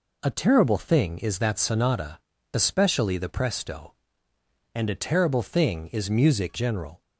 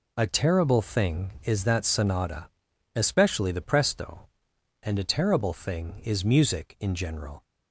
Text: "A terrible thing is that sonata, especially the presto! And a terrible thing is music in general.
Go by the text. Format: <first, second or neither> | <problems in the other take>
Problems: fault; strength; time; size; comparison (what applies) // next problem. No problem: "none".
second | skips "in"; at 6.5 s